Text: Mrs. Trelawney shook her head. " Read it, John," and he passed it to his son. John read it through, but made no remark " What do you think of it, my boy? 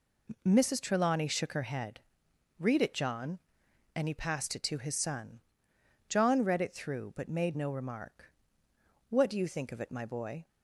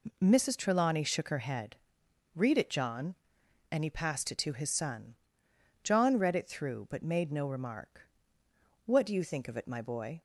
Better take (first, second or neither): neither